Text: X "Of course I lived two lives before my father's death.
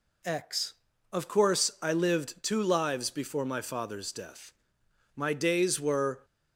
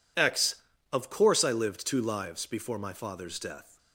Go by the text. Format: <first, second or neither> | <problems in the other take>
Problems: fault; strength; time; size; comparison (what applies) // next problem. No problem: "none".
second | goes on to say "My days were"; noticeable; from 5.1 s on; 1.1 s long